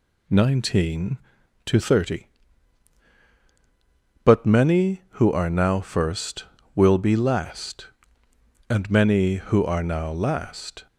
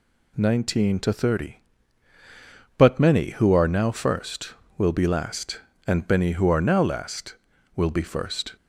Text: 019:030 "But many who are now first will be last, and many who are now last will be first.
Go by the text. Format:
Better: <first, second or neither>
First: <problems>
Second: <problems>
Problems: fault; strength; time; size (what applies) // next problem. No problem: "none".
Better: second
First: stops before "will be first"; at 10.8 s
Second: none